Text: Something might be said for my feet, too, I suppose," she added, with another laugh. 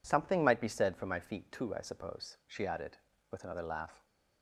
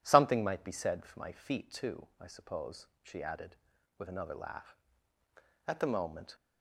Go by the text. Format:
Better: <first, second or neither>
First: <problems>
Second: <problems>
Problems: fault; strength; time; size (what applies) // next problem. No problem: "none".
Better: first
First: none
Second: goes on to say "At the moment"; noticeable; from 5.6 s on; 0.70 s long